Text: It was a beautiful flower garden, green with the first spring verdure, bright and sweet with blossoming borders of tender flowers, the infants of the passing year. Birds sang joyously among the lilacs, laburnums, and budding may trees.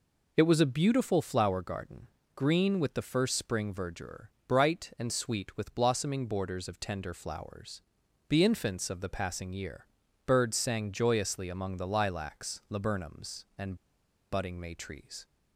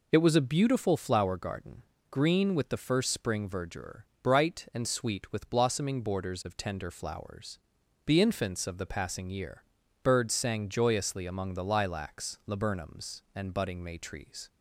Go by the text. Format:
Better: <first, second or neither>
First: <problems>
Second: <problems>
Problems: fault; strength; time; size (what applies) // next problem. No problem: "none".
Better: second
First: pauses between "and" and "budding"; noticeable; at 13.7 s; 0.56 s long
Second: none